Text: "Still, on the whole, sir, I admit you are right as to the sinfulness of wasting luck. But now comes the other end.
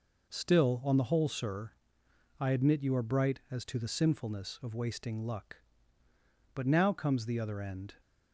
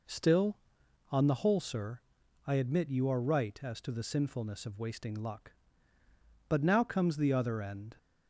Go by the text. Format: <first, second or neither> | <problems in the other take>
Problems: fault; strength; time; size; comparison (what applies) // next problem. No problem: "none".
second | says "bright" for "right"; at 3.0 s